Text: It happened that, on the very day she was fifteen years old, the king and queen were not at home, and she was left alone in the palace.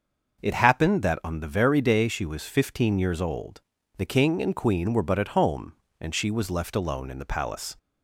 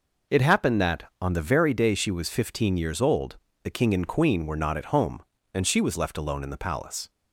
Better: second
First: starts louder than the rest; noticeable; until 1.4 s; 6 dB // says "but" for "not"; at 5.0 s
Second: none

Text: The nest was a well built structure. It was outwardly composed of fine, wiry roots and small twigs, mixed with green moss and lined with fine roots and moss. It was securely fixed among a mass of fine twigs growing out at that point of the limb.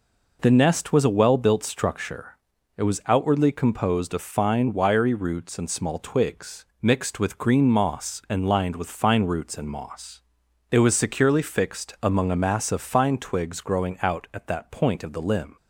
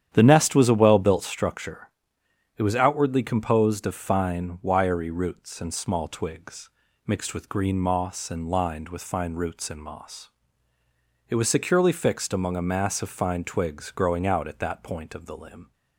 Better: first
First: none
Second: starts louder than the rest; strong; until 1.4 s; 9.5 dB

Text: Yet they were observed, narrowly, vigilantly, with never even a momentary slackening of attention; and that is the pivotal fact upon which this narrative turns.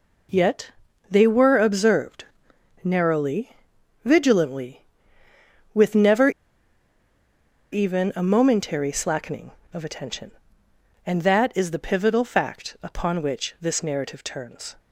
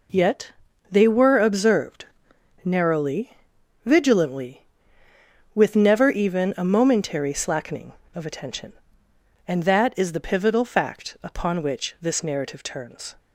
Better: second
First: pauses between "Yet" and "they"; at 0.6 s; 0.40 s long // pauses between "never" and "even"; strong; at 6.2 s; 1.4 s long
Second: pauses between "Yet" and "they"; at 0.5 s; 0.40 s long

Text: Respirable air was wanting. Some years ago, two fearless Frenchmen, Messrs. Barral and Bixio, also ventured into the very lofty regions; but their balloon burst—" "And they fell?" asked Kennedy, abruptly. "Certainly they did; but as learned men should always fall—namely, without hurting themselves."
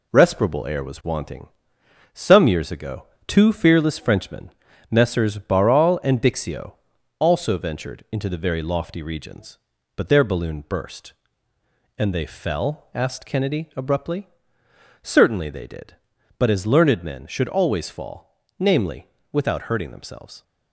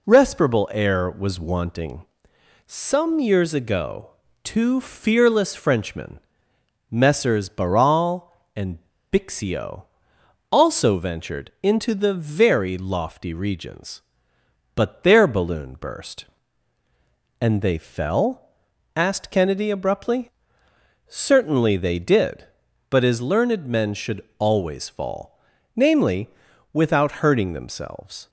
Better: first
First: none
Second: pauses between "and" and "Bixio"; slight; at 8.7 s; 0.31 s long

